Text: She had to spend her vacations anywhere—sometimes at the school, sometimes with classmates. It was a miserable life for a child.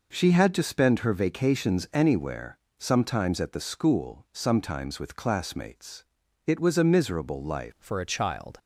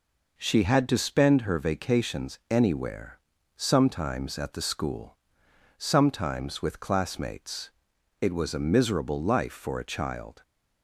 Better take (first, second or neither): second